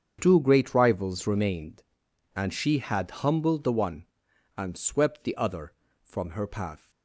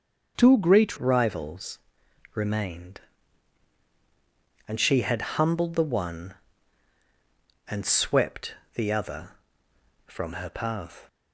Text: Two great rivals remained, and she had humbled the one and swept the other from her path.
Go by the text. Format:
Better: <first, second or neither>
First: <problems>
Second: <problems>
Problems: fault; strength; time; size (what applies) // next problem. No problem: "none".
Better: first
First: starts louder than the rest; strong; until 1.2 s; 7.5 dB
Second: starts louder than the rest; until 1.3 s; 6.5 dB // changes voice at "rivals"; from 0.9 s on; 10.1 s long // pauses between "rivals" and "remained"; noticeable; at 1.7 s; 0.54 s long // pauses between "swept" and "the"; slight; at 8.5 s; 0.20 s long